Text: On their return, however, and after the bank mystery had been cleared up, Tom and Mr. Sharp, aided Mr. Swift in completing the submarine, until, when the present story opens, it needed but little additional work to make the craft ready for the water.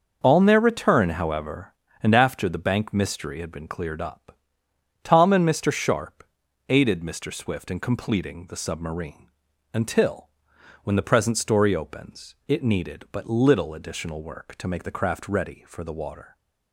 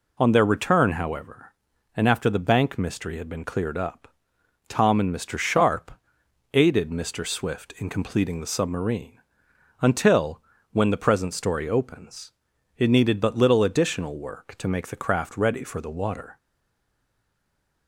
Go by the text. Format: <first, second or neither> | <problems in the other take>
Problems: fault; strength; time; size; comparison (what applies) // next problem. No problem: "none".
first | stays silent after the last word; noticeable; from 16.3 s on; 1.5 s long